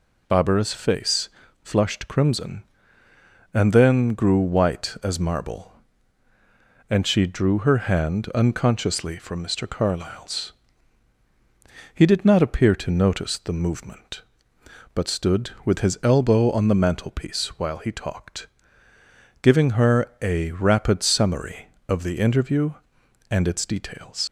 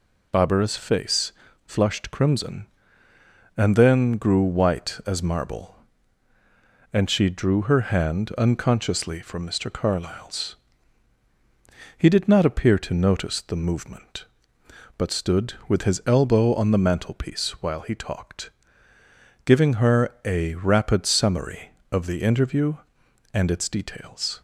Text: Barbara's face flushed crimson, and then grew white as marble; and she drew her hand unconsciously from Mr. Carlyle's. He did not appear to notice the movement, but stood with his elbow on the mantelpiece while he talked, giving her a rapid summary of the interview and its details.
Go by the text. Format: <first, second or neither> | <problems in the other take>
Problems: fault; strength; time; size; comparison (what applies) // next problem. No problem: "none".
second | pauses between "face" and "flushed"; slight; at 1.2 s; 0.32 s long; slight in the second // leaves "details" unfinished; at 24.2 s; 100 ms